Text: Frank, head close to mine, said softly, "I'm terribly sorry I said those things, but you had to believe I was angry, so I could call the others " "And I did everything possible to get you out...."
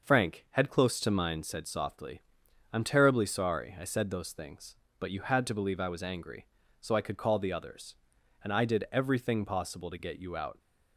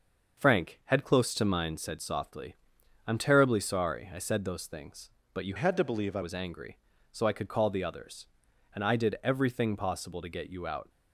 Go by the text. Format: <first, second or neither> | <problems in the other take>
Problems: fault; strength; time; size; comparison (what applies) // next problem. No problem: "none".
first | starts louder than the rest; noticeable; until 1.4 s; 6 dB; noticeable in the first // changes voice from "had" to "I"; from 5.5 to 6.2 s; 0.7 s long